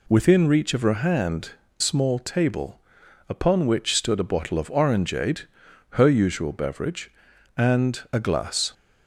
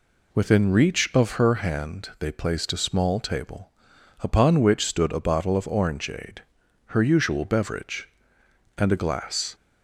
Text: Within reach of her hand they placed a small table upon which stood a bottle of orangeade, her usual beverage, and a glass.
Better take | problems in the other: second | skips "they placed a"; at 1.6 s // pauses between "table" and "upon"; noticeable; at 2.7 s; 0.50 s long; noticeable in the second

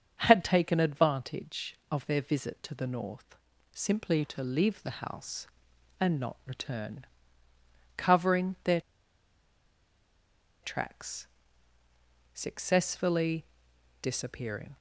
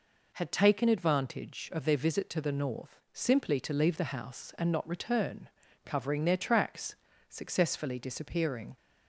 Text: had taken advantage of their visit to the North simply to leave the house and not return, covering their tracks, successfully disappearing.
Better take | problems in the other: second | starts louder than the rest; until 1.2 s; 7 dB // pauses between "North" and "simply"; slight; at 3.3 s; 0.36 s long // pauses between "their" and "tracks"; strong; at 8.7 s; 1.8 s long // pauses between "successfully" and "disappearing"; noticeable; at 13.4 s; 0.56 s long

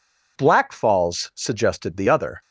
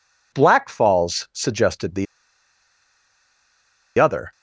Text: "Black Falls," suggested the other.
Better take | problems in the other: first | pauses between "the" and "other"; strong; at 2.0 s; 1.9 s long

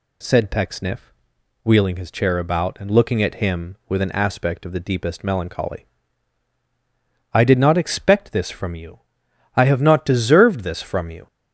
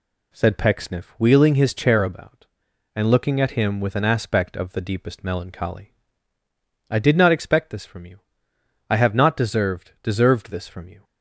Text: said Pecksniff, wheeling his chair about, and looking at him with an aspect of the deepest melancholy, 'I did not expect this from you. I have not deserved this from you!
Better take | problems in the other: first | says "deserved" twice; at 10.0 s

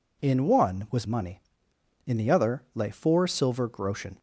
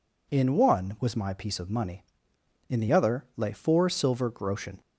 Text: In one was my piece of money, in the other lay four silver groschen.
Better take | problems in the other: second | skips "my piece of"; at 1.0 s

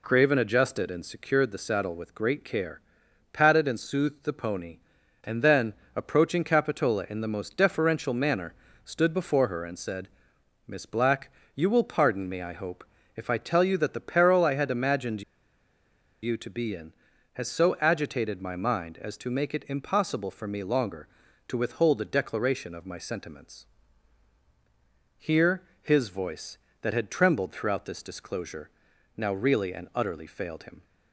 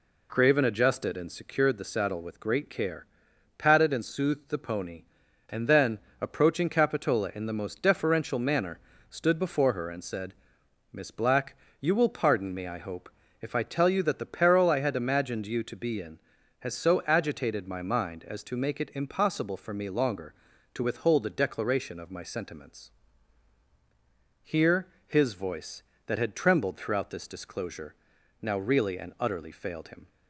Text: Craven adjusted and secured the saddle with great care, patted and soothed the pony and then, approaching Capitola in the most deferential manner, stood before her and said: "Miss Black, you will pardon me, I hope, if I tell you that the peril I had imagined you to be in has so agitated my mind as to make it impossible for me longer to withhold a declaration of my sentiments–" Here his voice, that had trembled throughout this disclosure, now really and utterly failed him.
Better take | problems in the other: second | pauses between "imagined" and "you"; at 15.2 s; 1.0 s long // pauses between "Here" and "his"; slight; at 25.6 s; 0.18 s long; slight in the second

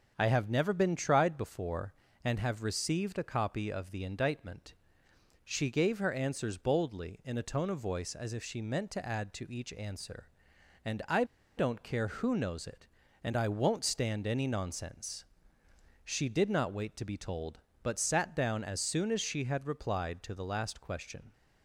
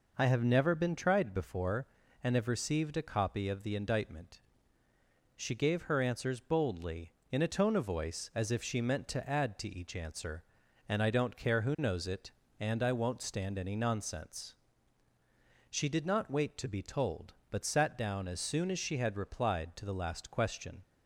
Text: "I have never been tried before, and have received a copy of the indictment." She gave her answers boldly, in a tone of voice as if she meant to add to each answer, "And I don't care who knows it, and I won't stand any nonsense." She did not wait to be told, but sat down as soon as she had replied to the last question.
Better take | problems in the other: second | starts louder than the rest; until 1.1 s; 6.5 dB // pauses between "I" and "don't"; slight; at 11.2 s; 0.33 s long

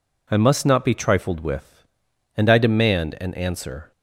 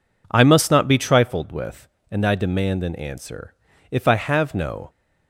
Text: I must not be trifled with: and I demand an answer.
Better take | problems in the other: first | goes on to say "If I have no"; noticeable; from 3.8 s on; 1.0 s long

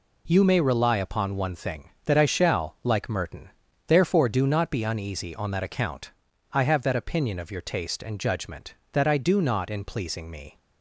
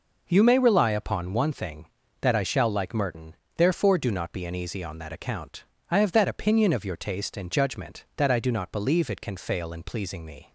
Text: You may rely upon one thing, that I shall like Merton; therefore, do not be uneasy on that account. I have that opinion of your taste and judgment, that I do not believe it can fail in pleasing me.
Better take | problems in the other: second | skips "believe it can fail"; at 9.7 s

